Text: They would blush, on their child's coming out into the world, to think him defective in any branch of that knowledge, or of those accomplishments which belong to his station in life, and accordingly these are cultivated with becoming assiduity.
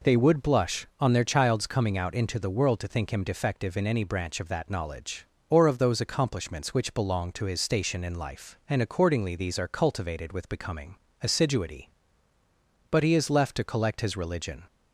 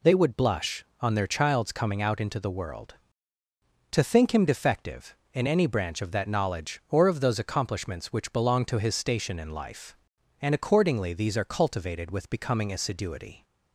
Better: second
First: pauses between "becoming" and "assiduity"; slight; at 10.9 s; 0.26 s long // goes on to say "But he is left to collect his religion"; strong; from 12.9 s on; 1.7 s long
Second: none

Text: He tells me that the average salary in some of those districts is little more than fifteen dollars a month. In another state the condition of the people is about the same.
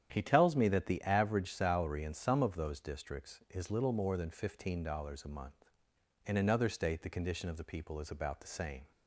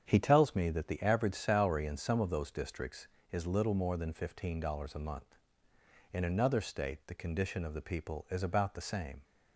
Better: neither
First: starts louder than the rest; strong; until 1.1 s; 9 dB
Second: starts louder than the rest; strong; until 1.0 s; 7.5 dB

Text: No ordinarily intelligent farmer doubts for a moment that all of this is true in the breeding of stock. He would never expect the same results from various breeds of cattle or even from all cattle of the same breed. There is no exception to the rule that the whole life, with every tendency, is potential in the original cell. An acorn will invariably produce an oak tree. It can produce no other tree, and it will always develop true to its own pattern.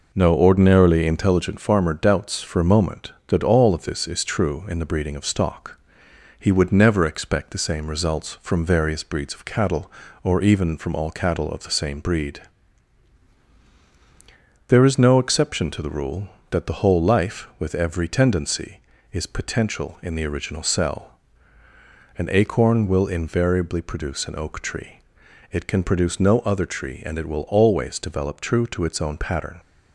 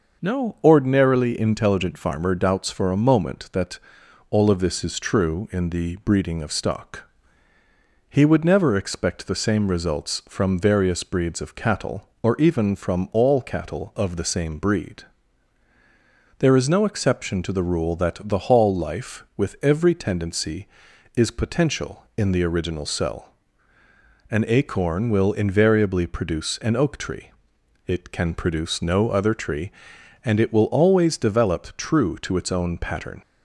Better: first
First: none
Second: pauses between "that" and "all"; noticeable; at 3.7 s; 0.52 s long // says "hall" for "whole"; at 18.3 s

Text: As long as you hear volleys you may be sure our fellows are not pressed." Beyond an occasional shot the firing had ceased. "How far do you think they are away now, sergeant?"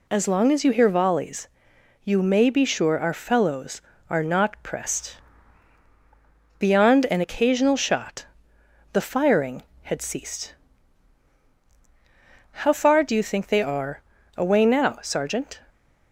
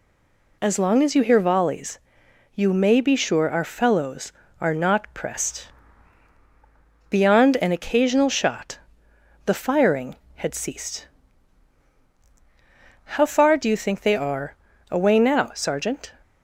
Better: first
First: pauses between "volleys" and "you"; noticeable; at 1.4 s; 0.56 s long // pauses between "shot" and "the"; noticeable; at 8.2 s; 0.66 s long // pauses between "are" and "away"; slight; at 14.0 s; 0.34 s long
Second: stays silent before the first word; slight; until 0.6 s; 0.6 s long // pauses between "volleys" and "you"; noticeable; at 1.9 s; 0.56 s long // pauses between "shot" and "the"; noticeable; at 8.7 s; 0.66 s long // pauses between "are" and "away"; slight; at 14.5 s; 0.34 s long

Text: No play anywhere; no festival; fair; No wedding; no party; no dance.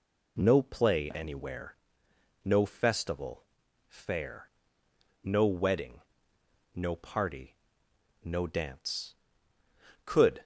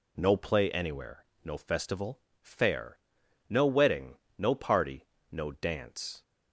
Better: second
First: goes on to say "Could"; slight; from 10.0 s on; 0.38 s long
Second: none

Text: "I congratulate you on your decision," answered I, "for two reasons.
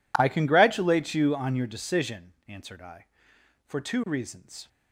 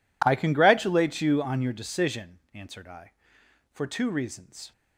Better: neither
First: none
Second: none

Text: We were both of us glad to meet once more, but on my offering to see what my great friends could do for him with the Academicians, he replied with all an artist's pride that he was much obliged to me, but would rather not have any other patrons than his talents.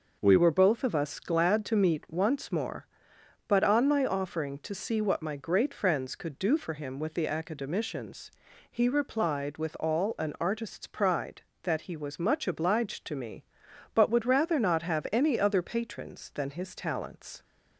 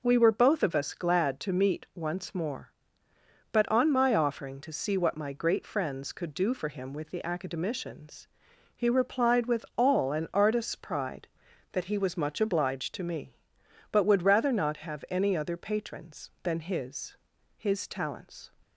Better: first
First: none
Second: says "his" twice; at 17.5 s

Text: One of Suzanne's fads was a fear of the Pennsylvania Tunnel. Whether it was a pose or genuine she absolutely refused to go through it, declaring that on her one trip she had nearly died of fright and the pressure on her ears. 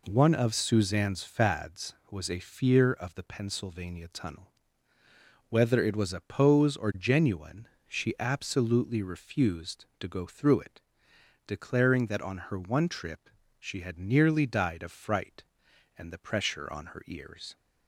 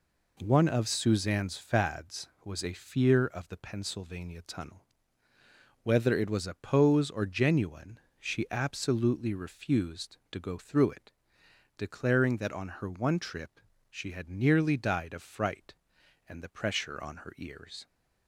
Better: neither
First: pauses between "genuine" and "she"; slight; at 7.6 s; 0.20 s long // pauses between "trip" and "she"; slight; at 13.2 s; 0.28 s long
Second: pauses between "genuine" and "she"; slight; at 7.9 s; 0.20 s long // pauses between "trip" and "she"; slight; at 13.5 s; 0.28 s long

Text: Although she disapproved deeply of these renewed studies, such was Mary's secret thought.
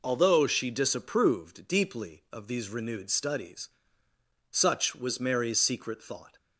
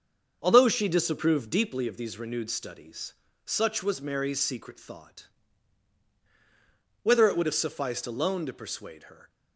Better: first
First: none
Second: starts louder than the rest; until 1.4 s; 6.5 dB // goes on to say "Whether it would have sufficed alone to persuade her"; strong; from 7.0 s on; 2.2 s long

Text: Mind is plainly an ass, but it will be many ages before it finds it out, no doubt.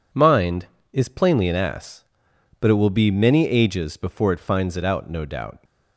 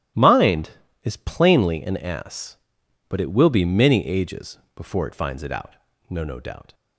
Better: first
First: none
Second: starts louder than the rest; strong; until 1.5 s; 13 dB // pauses between "ages" and "before"; slight; at 4.5 s; 0.16 s long // says "no" twice; at 6.2 s

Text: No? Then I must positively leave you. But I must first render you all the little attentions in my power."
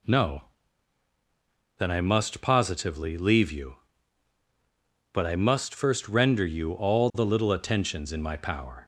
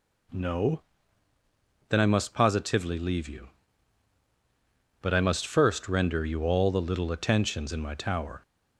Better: first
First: none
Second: says "tower" for "power"; at 7.9 s

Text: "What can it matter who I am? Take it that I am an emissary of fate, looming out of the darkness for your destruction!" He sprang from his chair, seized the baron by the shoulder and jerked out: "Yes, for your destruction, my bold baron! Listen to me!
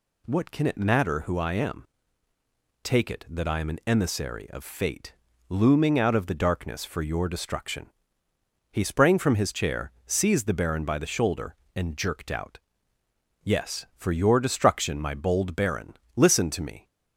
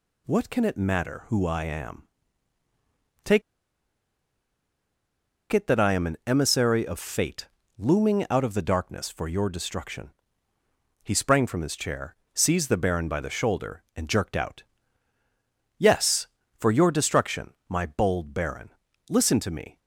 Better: first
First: none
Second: pauses between "Take" and "it"; strong; at 3.4 s; 2.1 s long

